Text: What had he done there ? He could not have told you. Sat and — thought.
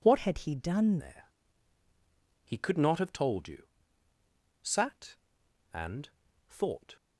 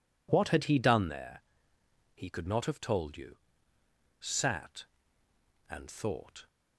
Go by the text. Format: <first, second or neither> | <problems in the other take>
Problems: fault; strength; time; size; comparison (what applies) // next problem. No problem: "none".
second | changes voice from "had" to "done"; from 0.1 to 0.9 s; 0.8 s long